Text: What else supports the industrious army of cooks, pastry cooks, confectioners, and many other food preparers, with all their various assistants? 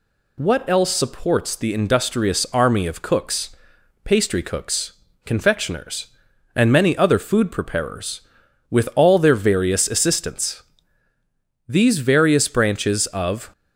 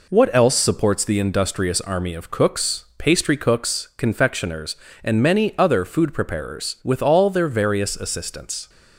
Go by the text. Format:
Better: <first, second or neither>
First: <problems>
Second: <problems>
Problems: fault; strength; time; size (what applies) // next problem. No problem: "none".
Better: second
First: goes on to say "These various branches of"; strong; from 11.6 s on; 1.8 s long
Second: none